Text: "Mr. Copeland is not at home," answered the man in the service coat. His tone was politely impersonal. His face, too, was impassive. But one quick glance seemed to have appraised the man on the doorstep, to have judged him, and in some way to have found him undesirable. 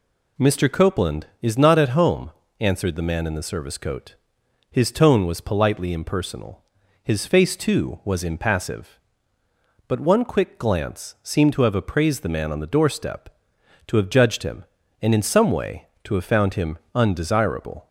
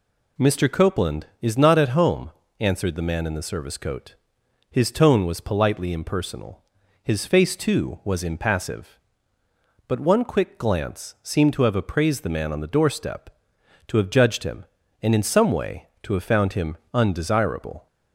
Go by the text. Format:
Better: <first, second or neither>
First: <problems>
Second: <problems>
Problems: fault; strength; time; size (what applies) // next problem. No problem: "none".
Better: neither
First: none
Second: none